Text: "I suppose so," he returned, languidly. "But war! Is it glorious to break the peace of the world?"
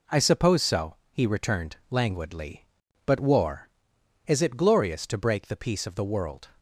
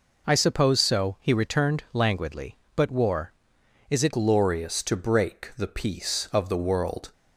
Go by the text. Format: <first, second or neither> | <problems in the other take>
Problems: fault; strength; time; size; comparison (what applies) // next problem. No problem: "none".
first | changes voice at "glorious"; from 4.1 s on; 3.0 s long